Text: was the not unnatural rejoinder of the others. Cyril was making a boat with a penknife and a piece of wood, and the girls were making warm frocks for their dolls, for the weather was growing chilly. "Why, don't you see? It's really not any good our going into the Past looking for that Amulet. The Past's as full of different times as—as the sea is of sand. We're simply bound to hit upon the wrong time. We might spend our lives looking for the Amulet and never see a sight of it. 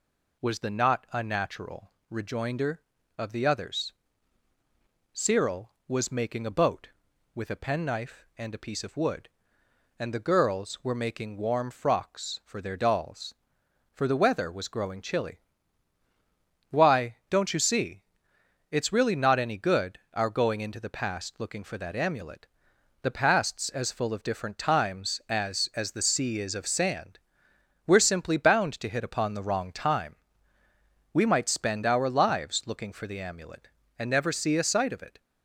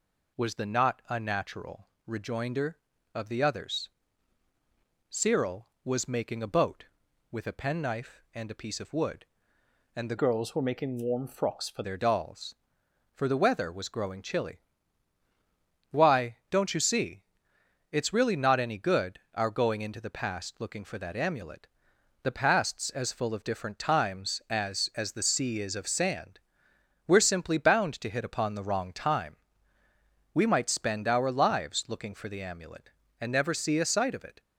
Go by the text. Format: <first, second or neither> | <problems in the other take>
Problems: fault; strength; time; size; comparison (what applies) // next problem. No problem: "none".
first | pauses between "unnatural" and "rejoinder"; slight; at 1.8 s; 0.18 s long; slight in the first // changes voice from "girls" to "for"; from 10.1 to 11.8 s; 1.7 s long